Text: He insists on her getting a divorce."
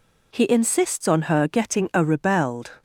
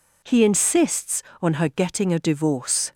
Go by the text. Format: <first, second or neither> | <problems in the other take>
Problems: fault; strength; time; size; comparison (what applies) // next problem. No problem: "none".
second | says "rebelled" for "divorce"; at 2.0 s